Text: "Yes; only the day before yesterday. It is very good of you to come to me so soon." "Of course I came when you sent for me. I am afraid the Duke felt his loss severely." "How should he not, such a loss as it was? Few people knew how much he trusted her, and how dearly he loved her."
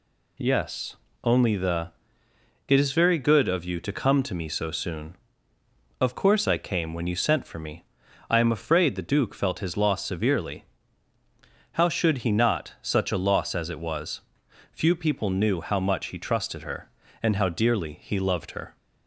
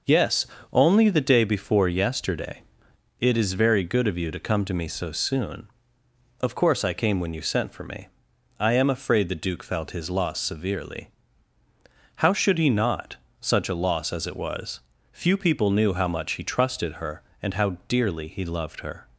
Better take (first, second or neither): second